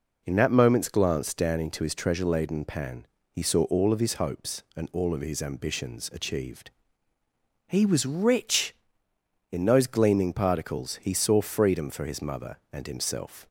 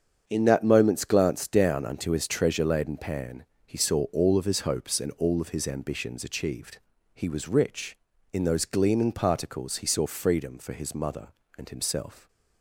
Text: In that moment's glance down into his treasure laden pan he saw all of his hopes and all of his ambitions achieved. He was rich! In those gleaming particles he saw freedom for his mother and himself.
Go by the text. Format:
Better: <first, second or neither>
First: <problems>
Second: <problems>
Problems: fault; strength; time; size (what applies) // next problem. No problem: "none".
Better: first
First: pauses between "pan" and "he"; slight; at 3.0 s; 0.28 s long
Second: starts louder than the rest; strong; until 1.2 s; 7.5 dB // says "unto" for "into"; at 1.8 s // pauses between "pan" and "he"; slight; at 3.4 s; 0.18 s long